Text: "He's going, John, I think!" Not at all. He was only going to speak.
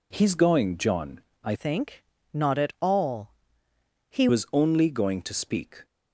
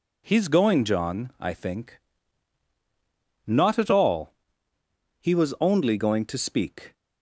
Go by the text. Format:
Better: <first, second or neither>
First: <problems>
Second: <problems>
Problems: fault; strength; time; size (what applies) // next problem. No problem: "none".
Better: second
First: changes voice from "think" to "He"; from 1.5 to 4.2 s; 2.7 s long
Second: none